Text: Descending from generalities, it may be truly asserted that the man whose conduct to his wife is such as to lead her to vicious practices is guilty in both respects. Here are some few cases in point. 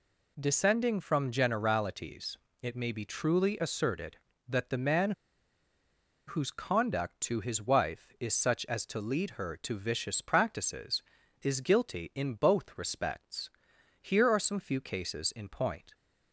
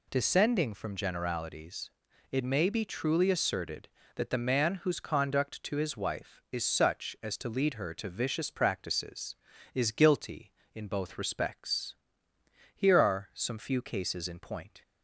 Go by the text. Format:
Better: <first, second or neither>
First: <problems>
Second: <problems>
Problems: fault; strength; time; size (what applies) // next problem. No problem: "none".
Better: second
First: pauses between "man" and "whose"; at 5.1 s; 1.1 s long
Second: none